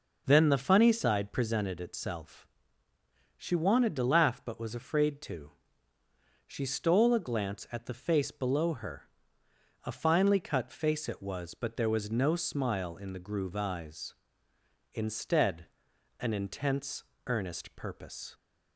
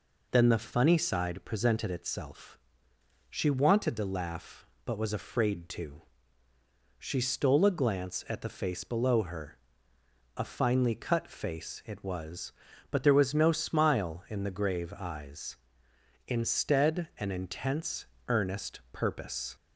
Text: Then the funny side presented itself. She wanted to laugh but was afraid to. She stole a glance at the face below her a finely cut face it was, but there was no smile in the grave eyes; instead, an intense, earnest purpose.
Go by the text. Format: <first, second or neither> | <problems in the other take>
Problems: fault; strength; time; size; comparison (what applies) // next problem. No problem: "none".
second | pauses between "her" and "a"; noticeable; at 9.0 s; 0.84 s long; noticeable in the second // says "groove" for "grave"; at 13.1 s